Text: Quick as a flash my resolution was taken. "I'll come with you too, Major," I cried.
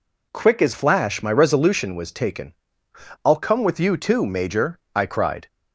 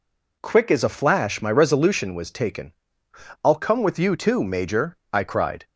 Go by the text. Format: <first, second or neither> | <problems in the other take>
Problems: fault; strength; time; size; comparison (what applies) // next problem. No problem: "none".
second | skips "a"; at 0.7 s